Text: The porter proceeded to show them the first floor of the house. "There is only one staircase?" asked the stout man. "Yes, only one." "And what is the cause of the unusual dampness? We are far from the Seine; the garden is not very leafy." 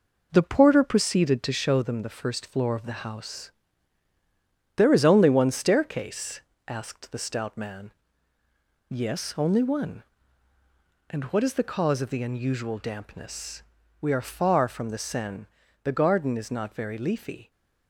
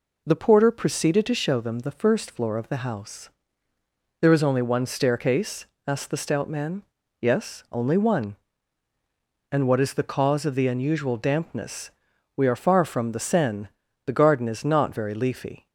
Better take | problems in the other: second | gets quieter; noticeable; throughout; 5.5 dB

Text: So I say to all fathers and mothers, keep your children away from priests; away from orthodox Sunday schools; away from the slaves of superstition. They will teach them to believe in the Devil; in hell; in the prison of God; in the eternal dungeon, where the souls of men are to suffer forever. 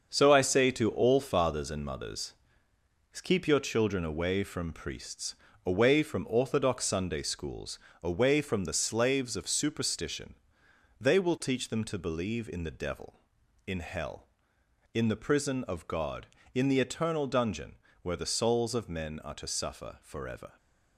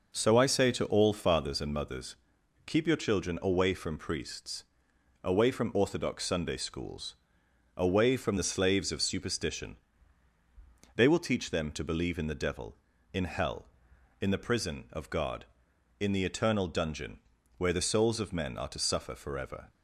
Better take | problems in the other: second | gets quieter; strong; throughout; 8 dB

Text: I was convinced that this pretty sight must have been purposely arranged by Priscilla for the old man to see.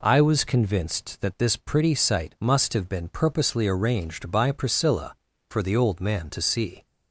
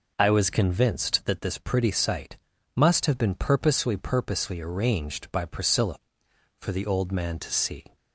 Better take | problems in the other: first | pauses between "sight" and "must"; at 2.3 s; 0.40 s long // says "purposely" twice; at 3.9 s

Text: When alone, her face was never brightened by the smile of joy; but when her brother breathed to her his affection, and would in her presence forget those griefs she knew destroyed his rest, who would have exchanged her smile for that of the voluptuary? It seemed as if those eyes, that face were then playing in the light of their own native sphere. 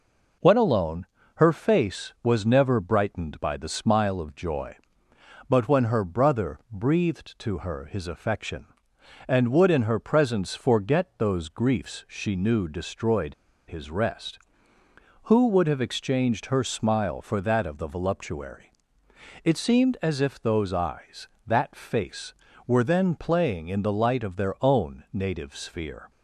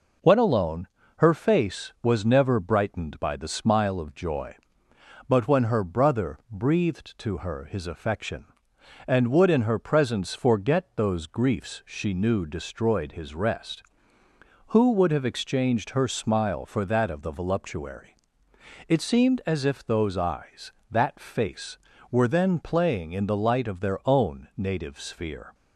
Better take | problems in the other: second | pauses between "destroyed" and "his"; slight; at 13.3 s; 0.33 s long

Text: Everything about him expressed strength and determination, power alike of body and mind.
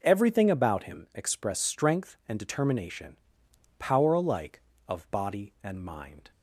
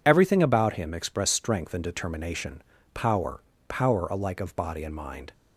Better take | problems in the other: first | says "power" twice; at 3.6 s

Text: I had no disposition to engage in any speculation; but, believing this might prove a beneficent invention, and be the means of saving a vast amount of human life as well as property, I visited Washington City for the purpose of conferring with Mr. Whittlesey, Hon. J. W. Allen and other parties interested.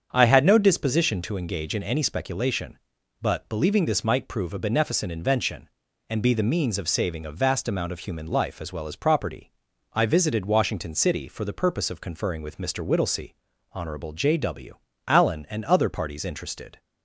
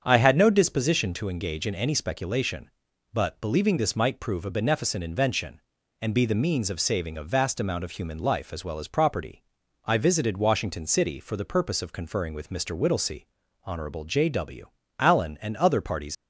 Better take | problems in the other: first | starts louder than the rest; strong; until 1.0 s; 7.5 dB; strong in the first // pauses between "W" and "Allen"; slight; at 14.6 s; 0.28 s long; slight in the first // stops before "interested"; at 16.1 s

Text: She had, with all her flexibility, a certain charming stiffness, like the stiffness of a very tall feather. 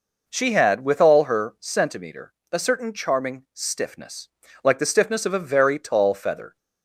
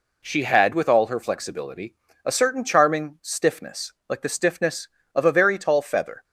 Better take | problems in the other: second | says "centimeter" for "flexibility"; at 1.6 s

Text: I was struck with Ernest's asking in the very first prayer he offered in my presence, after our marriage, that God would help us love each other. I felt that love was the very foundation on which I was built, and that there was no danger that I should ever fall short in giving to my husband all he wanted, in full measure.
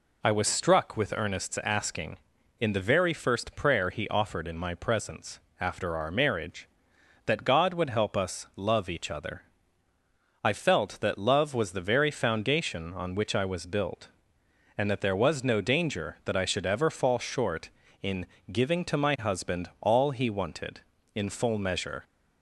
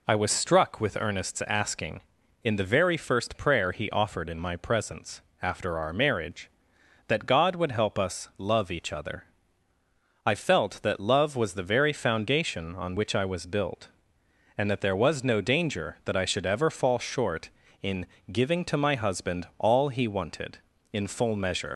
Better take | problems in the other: first | pauses between "in" and "giving"; slight; at 18.0 s; 0.26 s long; slight in the first // leaves "measure" unfinished; at 21.7 s; 65 ms

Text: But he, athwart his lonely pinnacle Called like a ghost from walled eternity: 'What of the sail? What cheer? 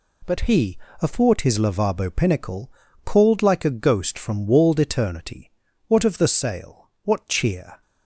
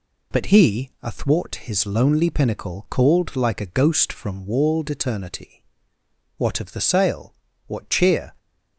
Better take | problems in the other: second | says "lavabo" for "lonely"; at 1.5 s // pauses between "pinnacle" and "Called"; slight; at 2.7 s; 0.33 s long

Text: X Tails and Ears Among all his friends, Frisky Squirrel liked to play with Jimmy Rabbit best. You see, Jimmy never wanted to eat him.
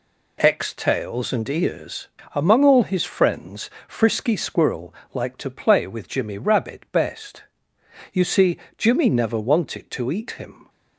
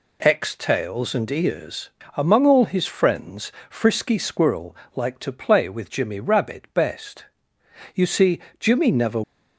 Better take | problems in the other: first | pauses between "Ears" and "Among"; slight; at 1.8 s; 0.26 s long; slight in the first // pauses between "Squirrel" and "liked"; slight; at 4.7 s; 0.20 s long; slight in the first // stops before "wanted to eat him"; at 9.2 s

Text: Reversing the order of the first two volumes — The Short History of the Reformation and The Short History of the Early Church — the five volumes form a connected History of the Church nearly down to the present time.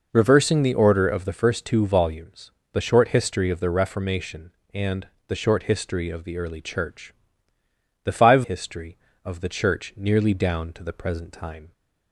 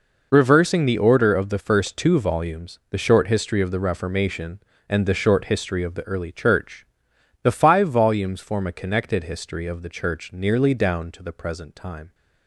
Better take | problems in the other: second | pauses between "and" and "The"; slight; at 5.0 s; 0.22 s long // skips "volumes form a connected"; at 8.4 s

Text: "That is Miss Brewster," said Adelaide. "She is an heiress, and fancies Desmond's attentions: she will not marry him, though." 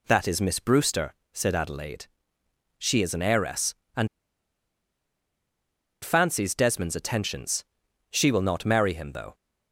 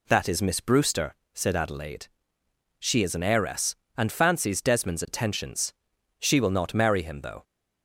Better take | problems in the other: second | pauses between "and" and "fancies"; strong; at 4.0 s; 1.9 s long

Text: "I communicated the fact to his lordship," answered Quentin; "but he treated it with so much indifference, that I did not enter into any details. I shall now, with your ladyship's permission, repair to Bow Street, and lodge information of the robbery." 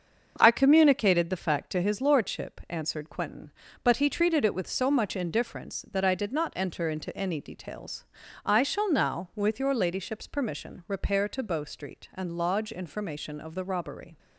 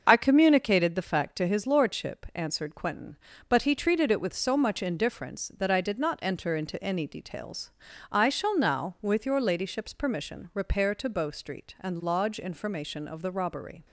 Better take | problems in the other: first | loses the start of "I"; at 0.0 s; 55 ms // starts louder than the rest; until 1.0 s; 6.5 dB; also in the first

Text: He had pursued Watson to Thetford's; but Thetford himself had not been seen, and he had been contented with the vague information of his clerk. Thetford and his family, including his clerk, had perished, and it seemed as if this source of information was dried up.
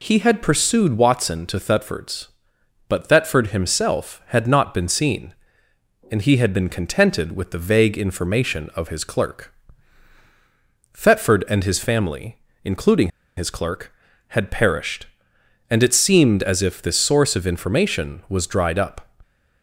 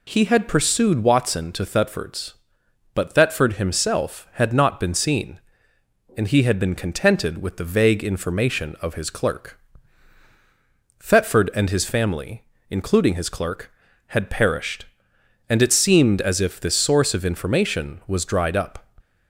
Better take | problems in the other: second | pauses between "including" and "his"; slight; at 13.1 s; 0.27 s long

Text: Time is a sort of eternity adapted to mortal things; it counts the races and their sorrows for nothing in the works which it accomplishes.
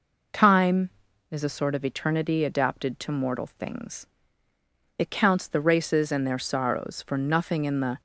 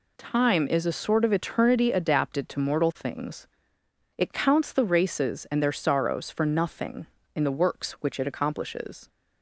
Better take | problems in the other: second | stops before "works which it accomplishes"; at 7.9 s

